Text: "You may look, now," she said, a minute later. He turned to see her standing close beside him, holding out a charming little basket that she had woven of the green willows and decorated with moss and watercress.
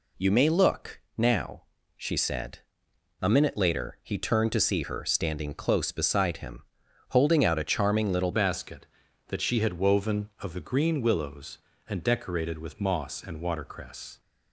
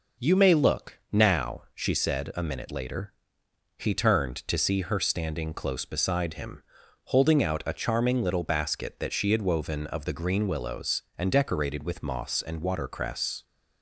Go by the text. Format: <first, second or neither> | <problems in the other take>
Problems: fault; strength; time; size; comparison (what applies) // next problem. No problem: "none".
second | changes voice at "basket"; from 8.3 s on; 5.8 s long